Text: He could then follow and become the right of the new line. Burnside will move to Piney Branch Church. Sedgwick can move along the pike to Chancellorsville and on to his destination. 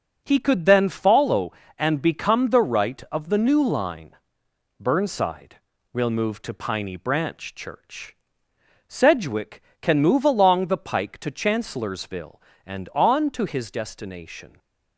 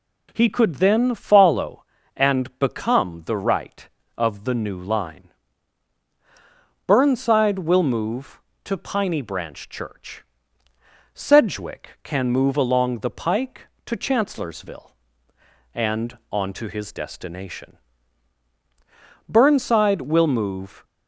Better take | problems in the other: first | goes on to say "Burnside will move"; from 19.2 s on; 1.5 s long

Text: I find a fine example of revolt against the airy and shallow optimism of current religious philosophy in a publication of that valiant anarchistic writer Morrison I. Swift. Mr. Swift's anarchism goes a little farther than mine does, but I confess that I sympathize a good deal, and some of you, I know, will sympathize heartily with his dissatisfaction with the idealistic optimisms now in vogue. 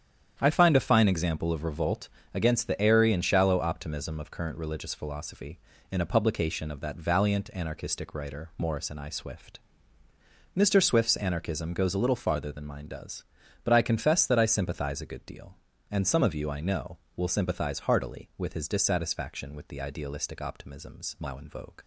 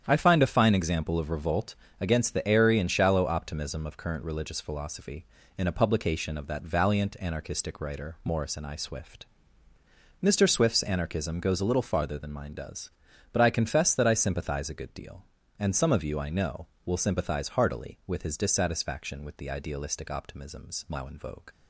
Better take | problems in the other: neither | starts louder than the rest; strong; the same in both // pauses between "revolt" and "against"; slight; the same in both

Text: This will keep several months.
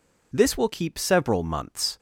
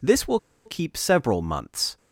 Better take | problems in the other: first | pauses between "will" and "keep"; slight; at 0.3 s; 0.26 s long

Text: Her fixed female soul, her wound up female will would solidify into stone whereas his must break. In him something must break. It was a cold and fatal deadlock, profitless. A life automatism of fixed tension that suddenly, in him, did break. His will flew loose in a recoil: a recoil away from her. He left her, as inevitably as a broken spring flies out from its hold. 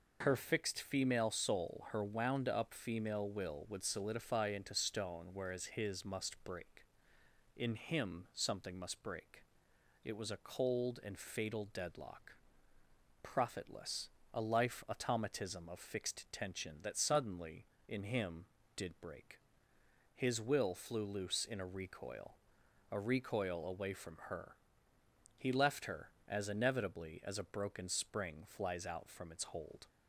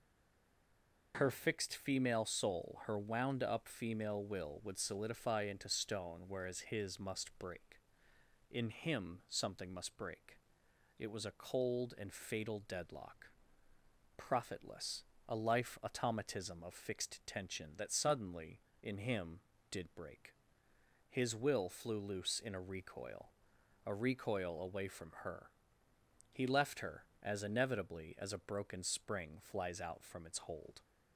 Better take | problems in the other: first | stays silent before the first word; until 1.1 s; 1.1 s long

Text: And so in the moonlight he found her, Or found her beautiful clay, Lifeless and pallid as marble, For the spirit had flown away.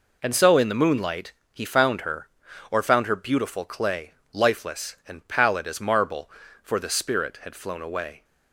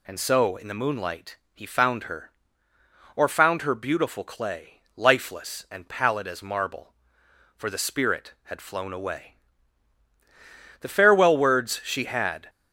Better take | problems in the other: first | pauses between "moonlight" and "he"; slight; at 1.3 s; 0.16 s long; slight in the first // goes on to say "The farewell words she had"; strong; from 10.8 s on; 1.6 s long

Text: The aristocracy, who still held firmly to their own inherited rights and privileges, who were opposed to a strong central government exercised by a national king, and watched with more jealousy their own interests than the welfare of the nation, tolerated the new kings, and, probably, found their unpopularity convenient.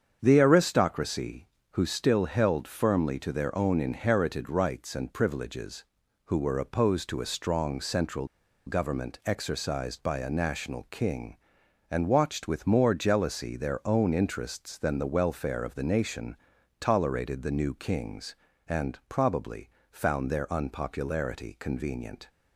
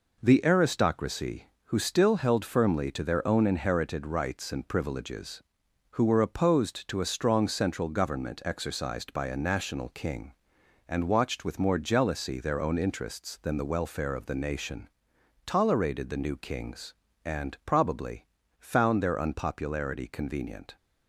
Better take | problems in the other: second | starts louder than the rest; strong; until 1.2 s; 7.5 dB // pauses between "central" and "government"; at 8.2 s; 0.39 s long

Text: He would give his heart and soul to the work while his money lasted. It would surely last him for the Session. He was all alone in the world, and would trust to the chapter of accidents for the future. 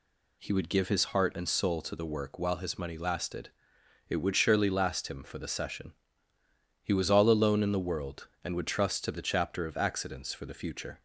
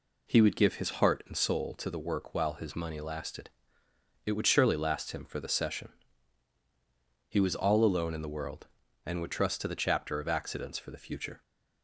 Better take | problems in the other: neither | none

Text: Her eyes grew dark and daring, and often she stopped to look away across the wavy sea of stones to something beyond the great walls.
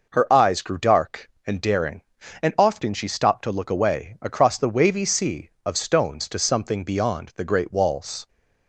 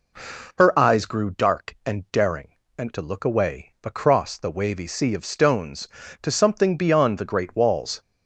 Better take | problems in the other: first | skips "often she stopped"; at 2.9 s

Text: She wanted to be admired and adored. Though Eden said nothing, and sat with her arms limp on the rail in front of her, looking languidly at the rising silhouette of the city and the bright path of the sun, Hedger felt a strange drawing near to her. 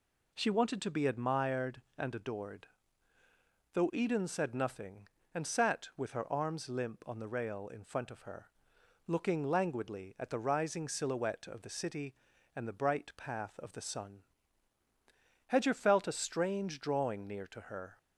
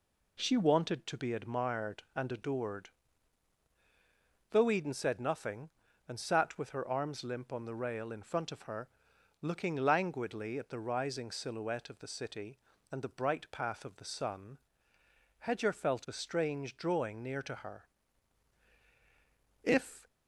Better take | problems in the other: first | goes on to say "If"; slight; from 19.6 s on; 0.44 s long

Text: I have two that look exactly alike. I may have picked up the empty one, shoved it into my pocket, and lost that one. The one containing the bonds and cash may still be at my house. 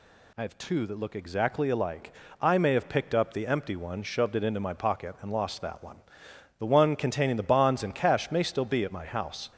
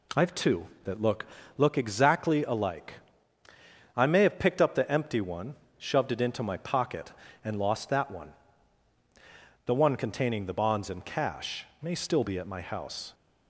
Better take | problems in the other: first | says "look" twice; at 1.5 s // pauses between "cash" and "may"; slight; at 11.6 s; 0.16 s long

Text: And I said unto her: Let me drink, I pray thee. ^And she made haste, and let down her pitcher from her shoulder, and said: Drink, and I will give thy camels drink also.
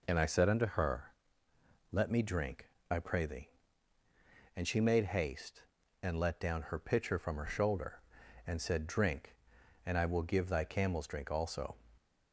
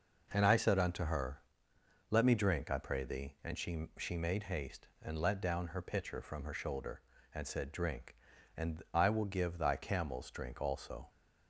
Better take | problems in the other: first | says "she" twice; at 3.9 s

